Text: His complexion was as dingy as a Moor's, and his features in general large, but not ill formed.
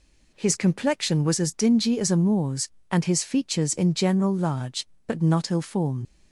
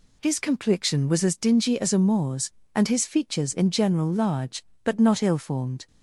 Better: second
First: leaves "formed" unfinished; at 6.0 s; 95 ms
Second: none

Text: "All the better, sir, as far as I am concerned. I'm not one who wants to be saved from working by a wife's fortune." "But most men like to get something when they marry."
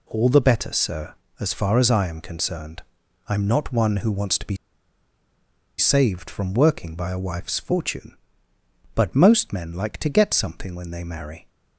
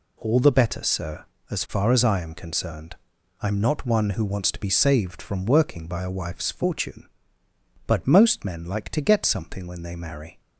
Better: second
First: pauses between "be" and "saved"; at 4.5 s; 1.2 s long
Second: none

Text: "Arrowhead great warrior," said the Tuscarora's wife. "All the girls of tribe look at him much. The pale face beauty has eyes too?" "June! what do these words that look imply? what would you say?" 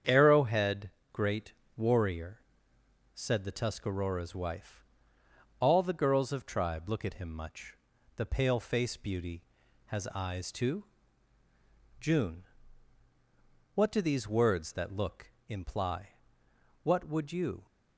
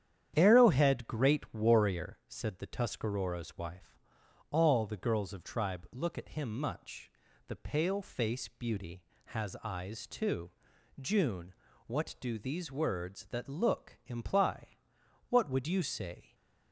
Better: second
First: starts louder than the rest; strong; until 1.2 s; 8 dB // pauses between "Arrowhead" and "great"; slight; at 0.9 s; 0.20 s long // pauses between "great" and "warrior"; slight; at 1.5 s; 0.22 s long // stops before "say"; at 17.6 s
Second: starts louder than the rest; strong; until 1.3 s; 9.5 dB

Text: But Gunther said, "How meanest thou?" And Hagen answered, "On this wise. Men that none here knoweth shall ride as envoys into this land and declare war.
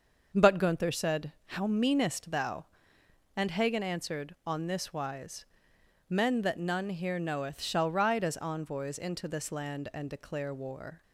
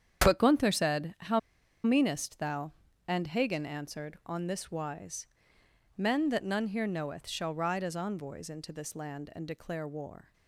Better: first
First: starts louder than the rest; until 1.4 s; 6.5 dB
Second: starts louder than the rest; strong; until 1.2 s; 8 dB // pauses between "How" and "meanest"; at 1.3 s; 0.44 s long

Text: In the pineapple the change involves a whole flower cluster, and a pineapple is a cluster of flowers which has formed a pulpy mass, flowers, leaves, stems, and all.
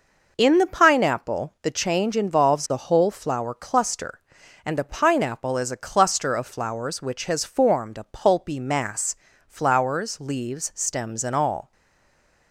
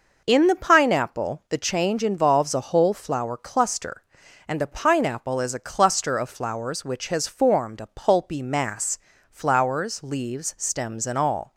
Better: second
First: stays silent after the last word; slight; from 11.7 s on; 0.8 s long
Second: none

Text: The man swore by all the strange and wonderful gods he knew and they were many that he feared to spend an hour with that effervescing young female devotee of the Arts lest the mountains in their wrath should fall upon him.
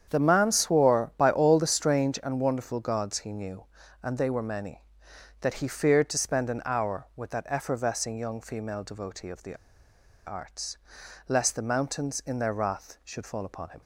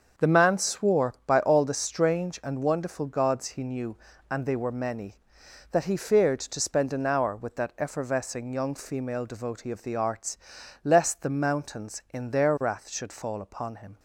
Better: second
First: starts louder than the rest; strong; until 1.1 s; 8 dB // pauses between "the" and "Arts"; noticeable; at 9.5 s; 0.72 s long // pauses between "Arts" and "lest"; noticeable; at 10.7 s; 0.50 s long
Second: starts louder than the rest; until 1.3 s; 7 dB // pauses between "Arts" and "lest"; noticeable; at 10.3 s; 0.46 s long

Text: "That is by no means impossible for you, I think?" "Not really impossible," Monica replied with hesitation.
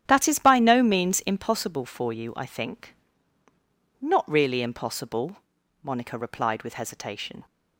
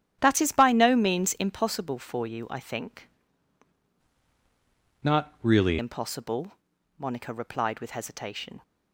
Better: first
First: starts louder than the rest; strong; until 1.0 s; 10.5 dB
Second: starts louder than the rest; strong; until 1.2 s; 10.5 dB // changes voice from "Not" to "really"; from 5.0 to 5.7 s; 0.7 s long

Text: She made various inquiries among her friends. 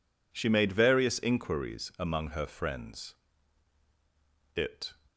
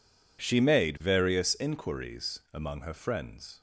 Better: second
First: goes on to say "It"; slight; from 4.5 s on; 0.38 s long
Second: none

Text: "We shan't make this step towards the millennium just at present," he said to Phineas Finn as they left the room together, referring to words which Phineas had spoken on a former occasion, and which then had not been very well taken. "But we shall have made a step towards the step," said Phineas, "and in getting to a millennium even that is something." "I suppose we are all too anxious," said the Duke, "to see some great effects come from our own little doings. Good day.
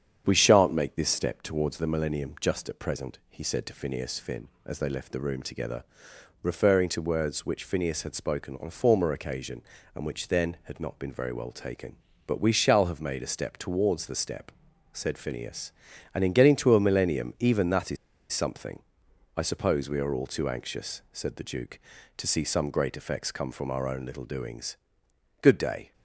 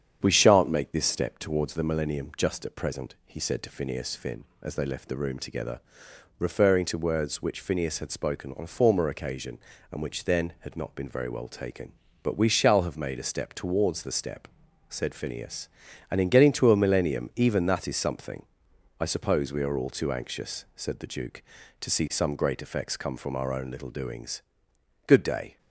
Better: second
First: starts louder than the rest; strong; until 1.2 s; 8 dB // pauses between "is" and "something"; slight; at 17.9 s; 0.36 s long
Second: starts louder than the rest; strong; until 1.2 s; 8 dB

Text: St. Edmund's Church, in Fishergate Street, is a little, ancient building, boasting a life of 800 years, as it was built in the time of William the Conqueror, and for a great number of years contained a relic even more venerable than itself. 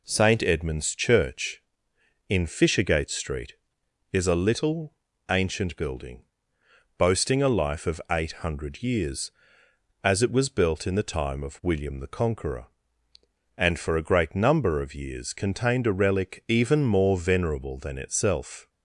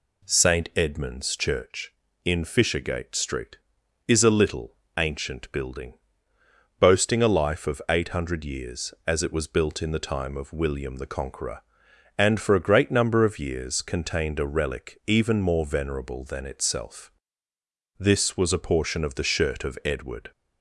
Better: first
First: none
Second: goes on to say "This was a portion of the shirt of Edward"; strong; from 17.9 s on; 2.3 s long

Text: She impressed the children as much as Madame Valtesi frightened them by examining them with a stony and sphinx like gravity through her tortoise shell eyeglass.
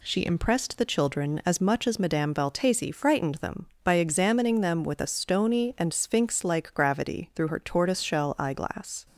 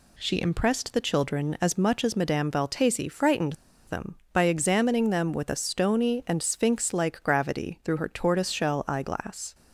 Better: first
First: none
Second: pauses between "frightened" and "them"; slight; at 3.5 s; 0.33 s long

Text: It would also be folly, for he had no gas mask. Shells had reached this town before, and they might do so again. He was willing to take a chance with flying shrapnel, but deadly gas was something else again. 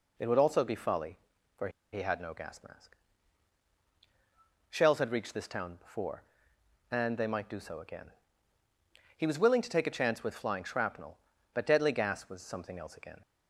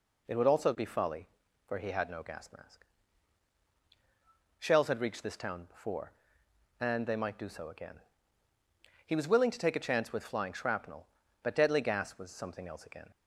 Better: second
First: pauses between "for" and "he"; slight; at 1.6 s; 0.23 s long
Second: none

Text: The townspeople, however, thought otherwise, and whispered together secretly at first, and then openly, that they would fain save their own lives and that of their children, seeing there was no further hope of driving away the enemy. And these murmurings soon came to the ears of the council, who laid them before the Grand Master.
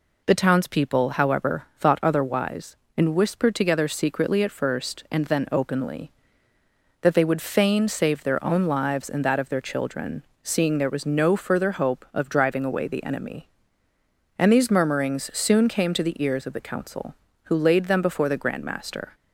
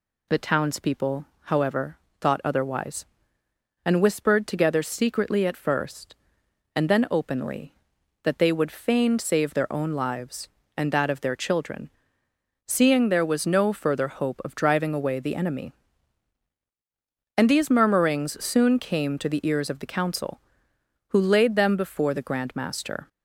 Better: neither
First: none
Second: none

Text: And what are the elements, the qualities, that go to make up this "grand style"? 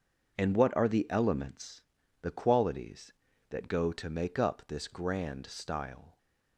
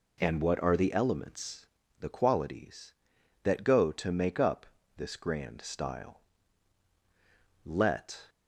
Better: first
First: none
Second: pauses between "up" and "this"; slight; at 4.6 s; 0.32 s long // goes on to say "Let"; noticeable; from 7.6 s on; 0.64 s long

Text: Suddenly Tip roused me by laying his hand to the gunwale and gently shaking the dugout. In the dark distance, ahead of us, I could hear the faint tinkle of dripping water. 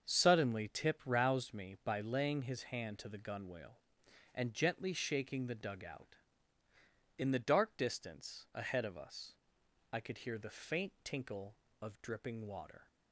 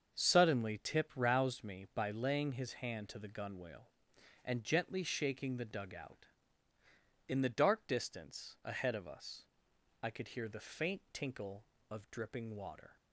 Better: neither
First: starts louder than the rest; until 1.1 s; 7 dB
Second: starts louder than the rest; until 1.2 s; 7 dB

